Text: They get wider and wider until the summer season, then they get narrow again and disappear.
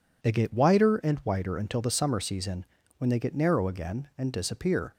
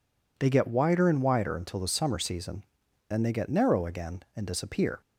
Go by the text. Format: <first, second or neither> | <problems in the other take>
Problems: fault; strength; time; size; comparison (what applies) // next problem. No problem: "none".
second | says "when" for "then"; at 2.9 s